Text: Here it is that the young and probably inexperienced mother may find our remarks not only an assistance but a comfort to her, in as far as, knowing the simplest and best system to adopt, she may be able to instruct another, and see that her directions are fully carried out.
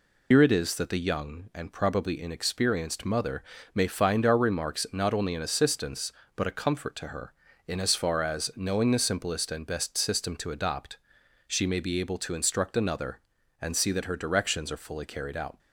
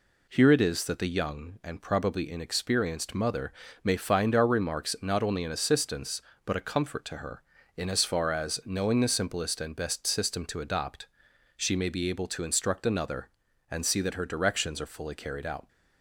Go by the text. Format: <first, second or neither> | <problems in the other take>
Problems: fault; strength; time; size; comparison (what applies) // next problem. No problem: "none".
second | loses the start of "Here"; at 0.3 s; 100 ms // pauses between "mother" and "may"; slight; at 3.4 s; 0.30 s long; slight in the second